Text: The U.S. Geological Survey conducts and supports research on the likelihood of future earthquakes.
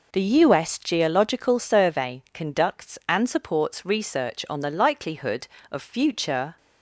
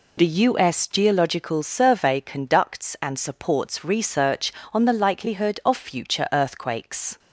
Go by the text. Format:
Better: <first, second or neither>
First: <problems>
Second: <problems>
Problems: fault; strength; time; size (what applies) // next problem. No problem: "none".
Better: second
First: stops before "earthquakes"; at 6.5 s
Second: none